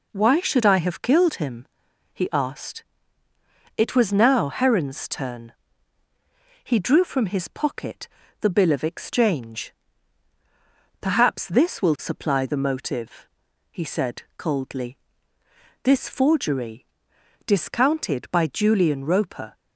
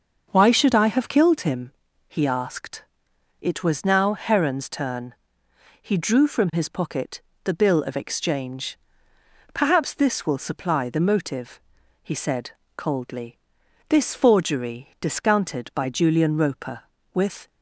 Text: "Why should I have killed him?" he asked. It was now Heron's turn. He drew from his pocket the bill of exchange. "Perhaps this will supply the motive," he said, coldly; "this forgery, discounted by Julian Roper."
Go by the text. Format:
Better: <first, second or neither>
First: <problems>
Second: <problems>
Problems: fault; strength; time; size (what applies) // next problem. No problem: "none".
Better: first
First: pauses between "pocket" and "the"; slight; at 8.0 s; 0.32 s long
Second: starts louder than the rest; until 1.3 s; 6 dB // pauses between "pocket" and "the"; slight; at 7.2 s; 0.22 s long // goes on to say "With"; slight; from 17.1 s on; 0.36 s long